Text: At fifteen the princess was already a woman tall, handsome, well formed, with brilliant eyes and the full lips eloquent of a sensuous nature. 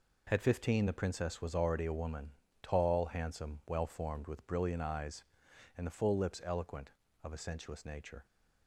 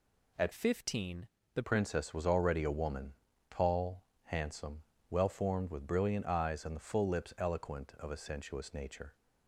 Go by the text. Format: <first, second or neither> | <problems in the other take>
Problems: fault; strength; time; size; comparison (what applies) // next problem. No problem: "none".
first | changes voice from "fifteen" to "the"; from 0.5 to 1.6 s; 1.1 s long // pauses between "fifteen" and "the"; slight; at 1.2 s; 0.28 s long // pauses between "woman" and "tall"; slight; at 3.1 s; 0.36 s long; slight in the first